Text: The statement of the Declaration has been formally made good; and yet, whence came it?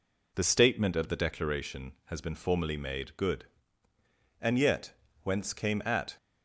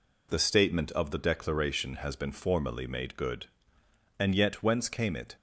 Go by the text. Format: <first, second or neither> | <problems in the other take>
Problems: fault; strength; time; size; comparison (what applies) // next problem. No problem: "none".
second | says "at" for "it"; at 5.8 s